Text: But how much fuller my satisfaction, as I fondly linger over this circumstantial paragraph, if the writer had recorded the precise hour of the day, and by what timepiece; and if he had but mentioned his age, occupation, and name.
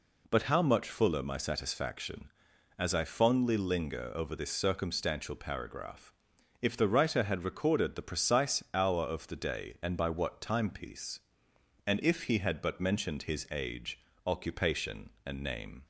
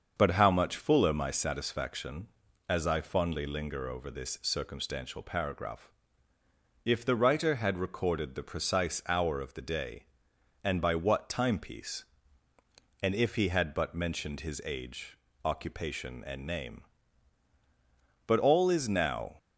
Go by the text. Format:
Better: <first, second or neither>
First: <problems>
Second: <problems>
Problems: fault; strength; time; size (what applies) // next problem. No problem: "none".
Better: first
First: none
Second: starts louder than the rest; until 1.1 s; 6.5 dB // goes on to say "But all is now"; noticeable; from 18.2 s on; 1.1 s long